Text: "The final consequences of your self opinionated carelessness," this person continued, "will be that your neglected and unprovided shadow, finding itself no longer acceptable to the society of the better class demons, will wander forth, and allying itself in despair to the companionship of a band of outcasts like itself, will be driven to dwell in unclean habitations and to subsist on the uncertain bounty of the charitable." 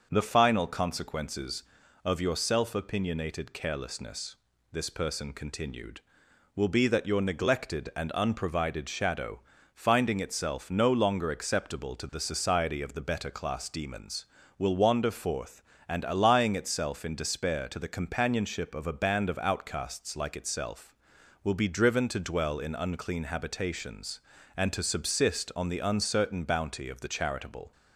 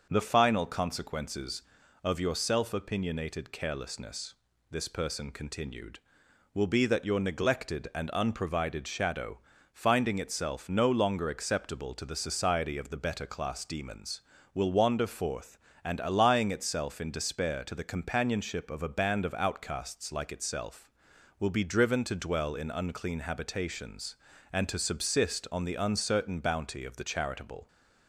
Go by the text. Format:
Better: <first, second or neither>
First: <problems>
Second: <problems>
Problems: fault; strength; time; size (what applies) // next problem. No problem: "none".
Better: neither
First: starts louder than the rest; until 1.1 s; 6 dB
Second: starts louder than the rest; until 1.1 s; 6 dB